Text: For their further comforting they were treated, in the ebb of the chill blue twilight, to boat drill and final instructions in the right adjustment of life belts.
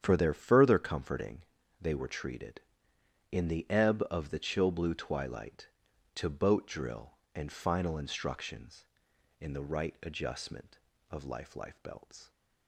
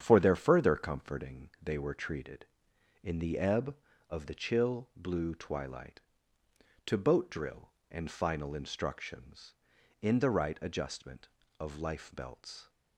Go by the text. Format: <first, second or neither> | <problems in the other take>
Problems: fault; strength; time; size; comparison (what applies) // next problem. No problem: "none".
second | starts louder than the rest; strong; until 1.0 s; 8.5 dB; strong in the second // pauses between "comforting" and "they"; at 1.4 s; 0.38 s long // says "life" twice; at 11.5 s